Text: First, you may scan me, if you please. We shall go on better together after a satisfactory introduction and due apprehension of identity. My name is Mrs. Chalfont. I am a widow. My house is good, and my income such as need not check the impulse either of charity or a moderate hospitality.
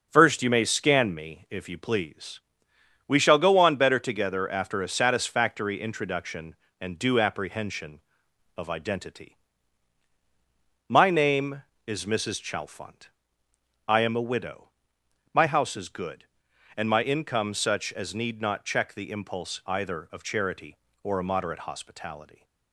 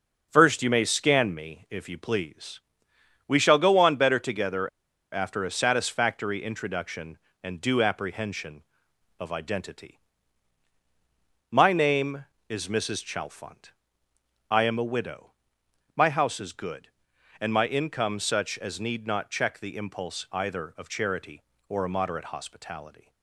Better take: first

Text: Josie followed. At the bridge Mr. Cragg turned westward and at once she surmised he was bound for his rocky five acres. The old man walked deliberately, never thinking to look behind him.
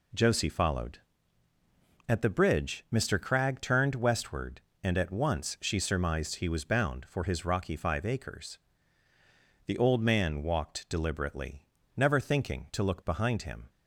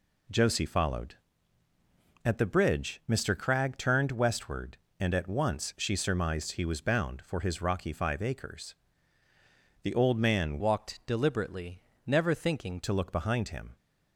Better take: first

